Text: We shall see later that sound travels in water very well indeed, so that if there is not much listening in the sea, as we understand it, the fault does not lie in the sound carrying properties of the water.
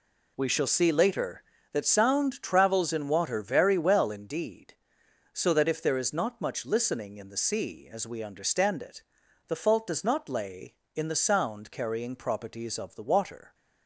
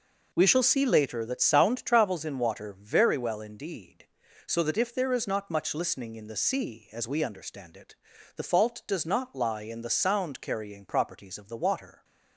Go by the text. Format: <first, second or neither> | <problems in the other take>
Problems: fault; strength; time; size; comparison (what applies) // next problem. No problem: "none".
second | says "lay" for "lie"; at 10.2 s